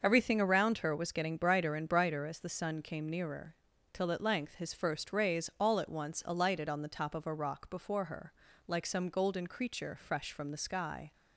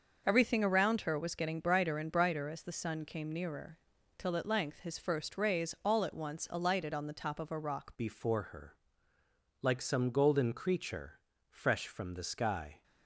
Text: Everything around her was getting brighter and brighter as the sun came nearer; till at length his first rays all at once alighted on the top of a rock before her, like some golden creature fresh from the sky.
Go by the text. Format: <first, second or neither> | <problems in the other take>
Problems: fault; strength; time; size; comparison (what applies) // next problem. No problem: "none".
first | starts louder than the rest; until 1.2 s; 6.5 dB; also in the first // changes voice at "before"; from 7.9 s on; 4.9 s long // pauses between "creature" and "fresh"; slight; at 11.1 s; 0.30 s long